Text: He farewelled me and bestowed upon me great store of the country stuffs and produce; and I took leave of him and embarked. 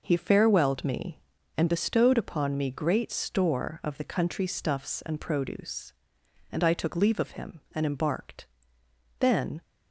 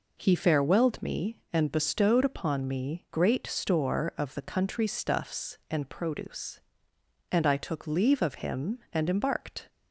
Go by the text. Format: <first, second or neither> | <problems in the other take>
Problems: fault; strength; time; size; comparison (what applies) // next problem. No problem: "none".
second | goes on to say "Then"; slight; from 9.2 s on; 0.42 s long